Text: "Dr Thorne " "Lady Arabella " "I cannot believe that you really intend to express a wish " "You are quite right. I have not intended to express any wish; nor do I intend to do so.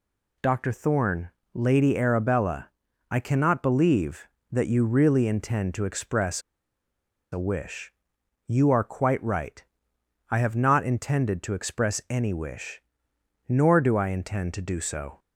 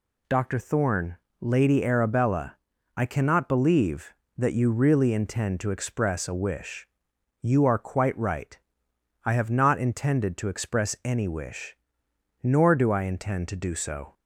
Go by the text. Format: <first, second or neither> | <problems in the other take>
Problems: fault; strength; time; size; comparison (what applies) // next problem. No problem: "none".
second | pauses between "express" and "a"; noticeable; at 6.4 s; 0.93 s long